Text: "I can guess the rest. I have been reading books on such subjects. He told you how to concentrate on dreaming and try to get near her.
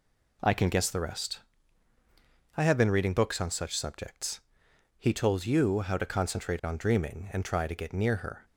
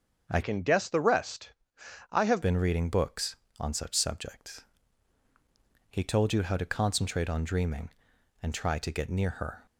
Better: first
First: none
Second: starts louder than the rest; until 1.3 s; 7 dB // changes voice from "can" to "have"; from 0.4 to 2.4 s; 2.0 s long

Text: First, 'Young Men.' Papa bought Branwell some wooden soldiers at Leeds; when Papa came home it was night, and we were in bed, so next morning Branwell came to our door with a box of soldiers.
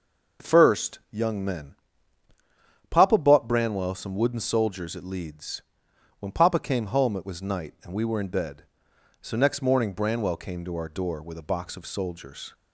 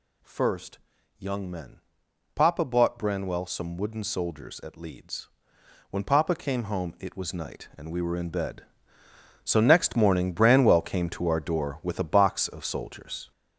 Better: first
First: none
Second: gets louder; throughout; 6.5 dB

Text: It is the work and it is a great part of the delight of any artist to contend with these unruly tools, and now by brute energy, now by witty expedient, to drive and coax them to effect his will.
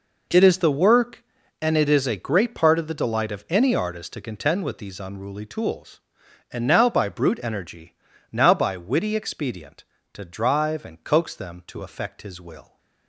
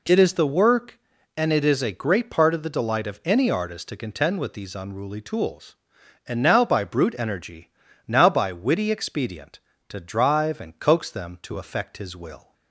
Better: second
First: gets quieter; strong; throughout; 13 dB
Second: none

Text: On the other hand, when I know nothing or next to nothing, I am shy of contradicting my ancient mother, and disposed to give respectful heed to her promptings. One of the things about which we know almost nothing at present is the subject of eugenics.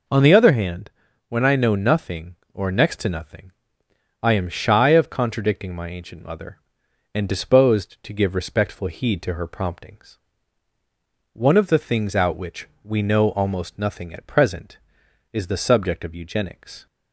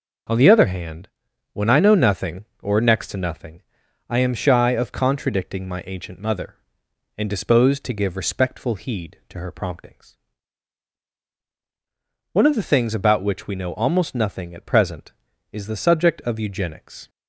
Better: second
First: says "out" for "about"; at 12.1 s // pauses between "which" and "we"; slight; at 12.6 s; 0.16 s long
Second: none

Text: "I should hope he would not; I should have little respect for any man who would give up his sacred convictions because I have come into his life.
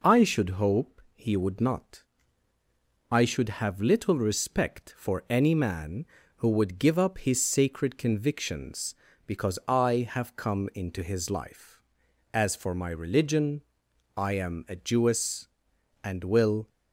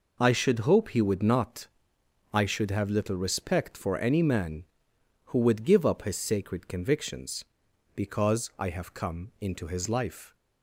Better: second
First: goes on to say "As for my religion I am a Jewess and will"; strong; from 12.3 s on; 4.3 s long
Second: none

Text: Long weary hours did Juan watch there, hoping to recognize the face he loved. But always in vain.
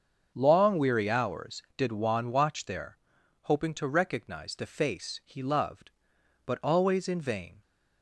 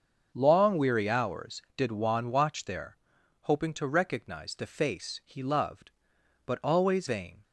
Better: first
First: starts louder than the rest; until 1.3 s; 7 dB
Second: starts louder than the rest; until 1.3 s; 7 dB // skips "in"; at 7.0 s

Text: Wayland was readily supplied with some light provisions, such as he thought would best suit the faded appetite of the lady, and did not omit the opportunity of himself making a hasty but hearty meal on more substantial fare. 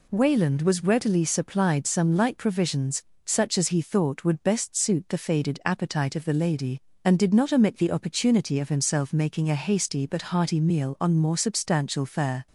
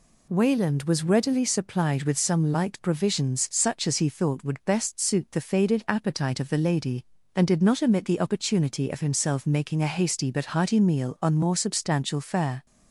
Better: second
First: skips "with"; at 1.8 s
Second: none

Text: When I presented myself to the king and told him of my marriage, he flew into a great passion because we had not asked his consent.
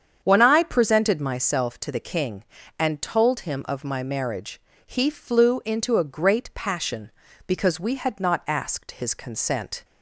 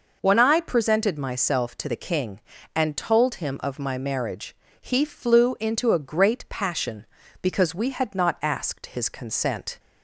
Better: second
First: starts louder than the rest; strong; until 1.4 s; 8 dB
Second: none

